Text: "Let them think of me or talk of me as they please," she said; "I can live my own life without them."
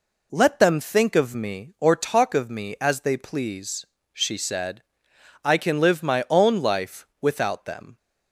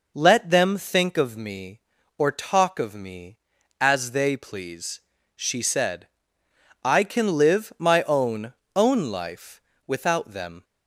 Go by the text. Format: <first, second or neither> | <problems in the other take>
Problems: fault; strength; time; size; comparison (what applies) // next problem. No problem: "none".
first | says "own" twice; at 8.7 s // pauses between "life" and "without"; slight; at 9.5 s; 0.26 s long